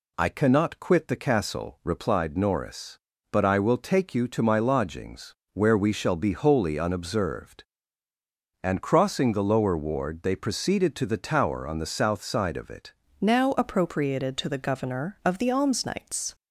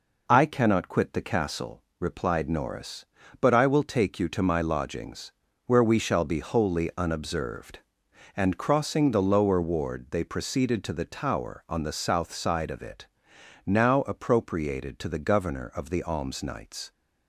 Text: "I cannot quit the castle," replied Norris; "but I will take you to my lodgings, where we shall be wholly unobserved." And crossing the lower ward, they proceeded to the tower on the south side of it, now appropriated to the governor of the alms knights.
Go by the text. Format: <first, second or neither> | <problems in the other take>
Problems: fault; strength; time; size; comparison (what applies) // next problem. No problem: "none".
second | changes voice at "now"; from 13.2 s on; 3.1 s long